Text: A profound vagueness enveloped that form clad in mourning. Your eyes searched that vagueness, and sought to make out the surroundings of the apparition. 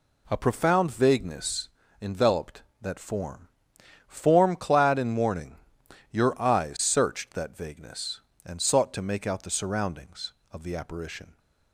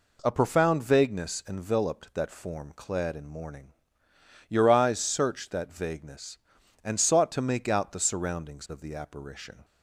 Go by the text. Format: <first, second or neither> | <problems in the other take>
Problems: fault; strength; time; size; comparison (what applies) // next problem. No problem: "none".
second | pauses between "vagueness" and "enveloped"; slight; at 1.6 s; 0.34 s long // says "form" twice; at 4.0 s